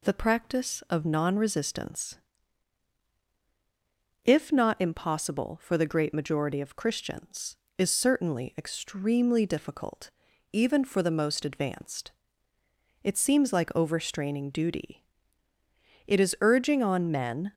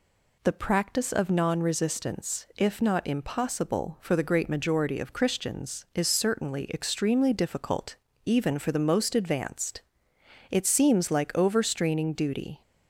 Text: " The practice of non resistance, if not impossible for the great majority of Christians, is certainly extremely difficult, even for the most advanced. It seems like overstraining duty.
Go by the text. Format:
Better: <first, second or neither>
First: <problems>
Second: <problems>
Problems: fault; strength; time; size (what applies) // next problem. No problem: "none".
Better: second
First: goes on to say "It is urging on men"; from 16.0 s on; 1.4 s long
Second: none